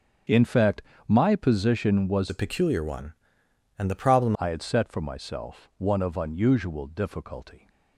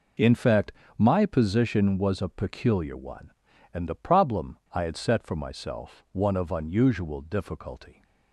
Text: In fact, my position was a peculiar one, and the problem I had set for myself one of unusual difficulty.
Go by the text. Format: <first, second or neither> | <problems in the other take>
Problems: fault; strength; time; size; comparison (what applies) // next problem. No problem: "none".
second | starts louder than the rest; strong; until 1.5 s; 7 dB // changes voice from "a" to "problem"; from 2.2 to 4.3 s; 2.1 s long